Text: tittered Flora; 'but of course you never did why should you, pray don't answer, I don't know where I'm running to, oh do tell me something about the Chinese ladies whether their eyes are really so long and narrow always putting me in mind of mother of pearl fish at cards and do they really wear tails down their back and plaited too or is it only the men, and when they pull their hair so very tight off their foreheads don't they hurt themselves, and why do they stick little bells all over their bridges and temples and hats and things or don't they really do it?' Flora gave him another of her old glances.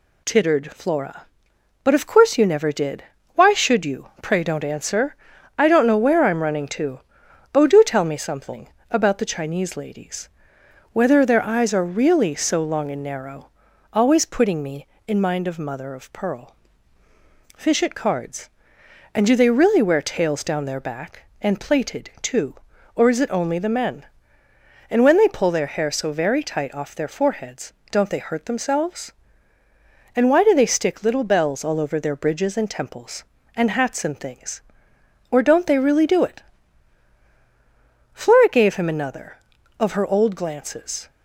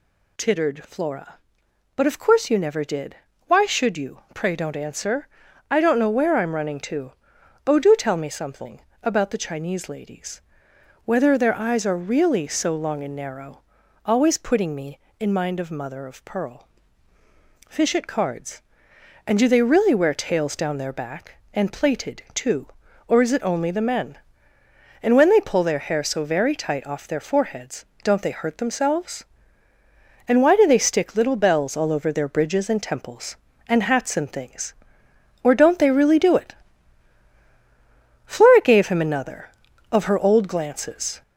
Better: first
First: pauses between "did" and "why"; slight; at 3.0 s; 0.32 s long // pauses between "something" and "about"; slight; at 8.6 s; 0.24 s long // pauses between "ladies" and "whether"; noticeable; at 10.2 s; 0.64 s long // pauses between "narrow" and "always"; noticeable; at 13.4 s; 0.46 s long // pauses between "pearl" and "fish"; at 16.5 s; 1.0 s long // pauses between "foreheads" and "don't"; slight; at 27.7 s; 0.20 s long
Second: gets louder; slight; throughout; 3.5 dB // pauses between "did" and "why"; slight; at 3.1 s; 0.32 s long // pauses between "something" and "about"; slight; at 8.7 s; 0.24 s long // pauses between "ladies" and "whether"; noticeable; at 10.3 s; 0.64 s long // pauses between "narrow" and "always"; noticeable; at 13.5 s; 0.46 s long // pauses between "pearl" and "fish"; at 16.6 s; 1.0 s long // pauses between "foreheads" and "don't"; slight; at 27.8 s; 0.20 s long

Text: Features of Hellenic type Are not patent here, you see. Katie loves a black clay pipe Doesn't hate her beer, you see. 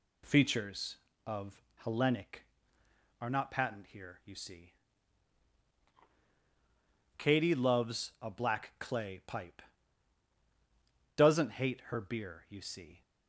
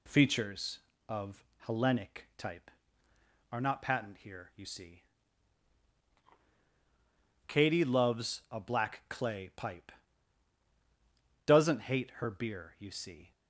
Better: second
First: pauses between "of" and "Hellenic"; slight; at 1.6 s; 0.20 s long // skips "type"; at 2.8 s // pauses between "pipe" and "Doesn't"; strong; at 9.6 s; 1.5 s long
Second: pauses between "of" and "Hellenic"; slight; at 1.4 s; 0.20 s long // pauses between "pipe" and "Doesn't"; strong; at 9.9 s; 1.5 s long

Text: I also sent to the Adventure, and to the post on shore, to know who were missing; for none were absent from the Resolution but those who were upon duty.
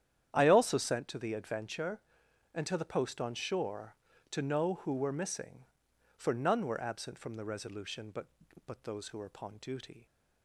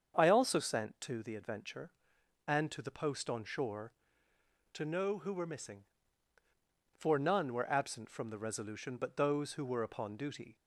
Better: second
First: starts louder than the rest; strong; until 1.3 s; 9.5 dB // says "but" twice; at 8.6 s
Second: starts louder than the rest; strong; until 1.1 s; 7 dB

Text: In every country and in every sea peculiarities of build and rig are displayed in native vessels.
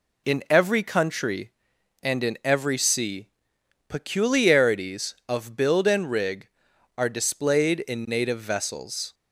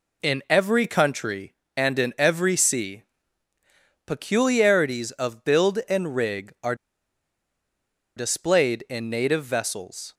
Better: first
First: pauses between "sea" and "peculiarities"; noticeable; at 3.2 s; 0.62 s long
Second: pauses between "sea" and "peculiarities"; at 3.0 s; 1.0 s long // pauses between "are" and "displayed"; strong; at 6.7 s; 1.4 s long

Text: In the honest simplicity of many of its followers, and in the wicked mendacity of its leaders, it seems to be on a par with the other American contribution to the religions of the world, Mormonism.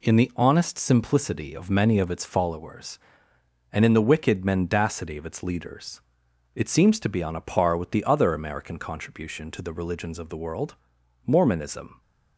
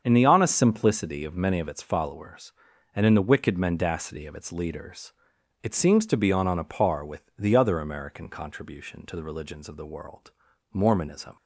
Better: first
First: none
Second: starts louder than the rest; until 1.0 s; 7 dB // says "on" twice; at 6.4 s

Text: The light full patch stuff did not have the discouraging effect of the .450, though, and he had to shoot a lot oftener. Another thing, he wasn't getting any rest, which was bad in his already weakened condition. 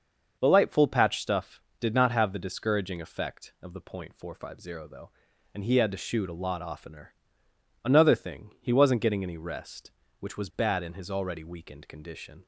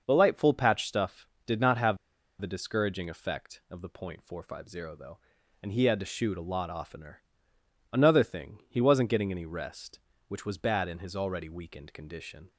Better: first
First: starts louder than the rest; until 1.4 s; 6 dB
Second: starts louder than the rest; until 1.0 s; 6 dB // pauses between "have" and "the"; at 1.9 s; 0.42 s long

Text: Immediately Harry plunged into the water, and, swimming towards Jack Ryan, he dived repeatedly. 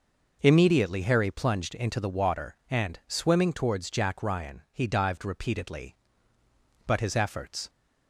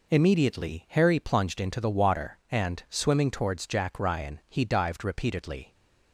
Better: second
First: goes on to say "But his efforts"; noticeable; from 6.8 s on; 0.82 s long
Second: none

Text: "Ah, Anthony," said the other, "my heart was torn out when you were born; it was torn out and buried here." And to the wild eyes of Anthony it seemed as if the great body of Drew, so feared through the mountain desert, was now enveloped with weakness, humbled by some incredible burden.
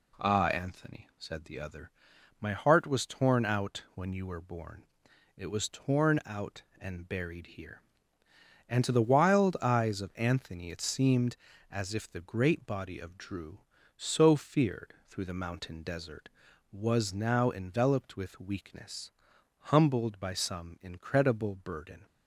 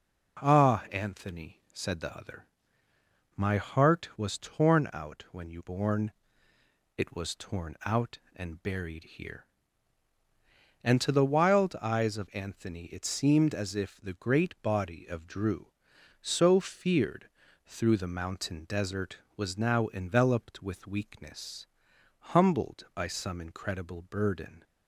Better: first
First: pauses between "feared" and "through"; slight; at 14.9 s; 0.16 s long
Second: skips "were"; at 5.6 s // pauses between "feared" and "through"; at 17.2 s; 0.38 s long

